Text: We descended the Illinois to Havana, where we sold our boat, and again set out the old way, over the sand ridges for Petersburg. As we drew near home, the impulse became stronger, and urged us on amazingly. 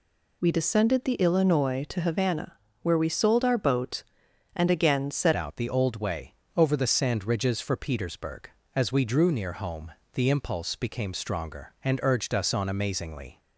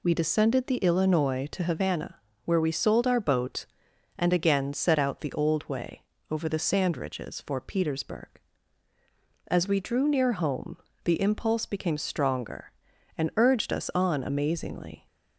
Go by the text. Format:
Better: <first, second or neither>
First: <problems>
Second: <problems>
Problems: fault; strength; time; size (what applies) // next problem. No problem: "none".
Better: second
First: changes voice at "out"; from 5.3 s on; 8.0 s long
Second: none